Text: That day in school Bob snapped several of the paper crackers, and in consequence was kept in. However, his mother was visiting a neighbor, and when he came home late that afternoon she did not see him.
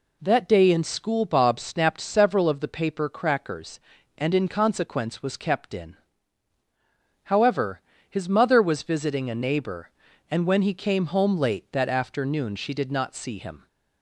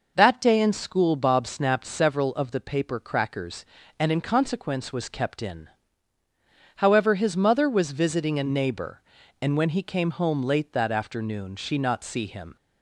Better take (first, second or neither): first